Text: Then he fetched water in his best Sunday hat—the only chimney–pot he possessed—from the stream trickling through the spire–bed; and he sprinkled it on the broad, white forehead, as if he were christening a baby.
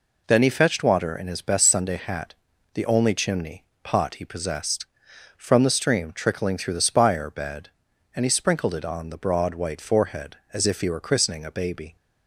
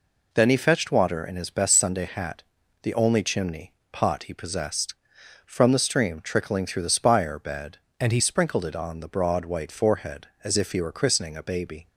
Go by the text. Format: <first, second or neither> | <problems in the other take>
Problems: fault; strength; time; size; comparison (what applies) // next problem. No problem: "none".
first | changes voice from "and" to "he"; from 7.9 to 8.2 s; 0.3 s long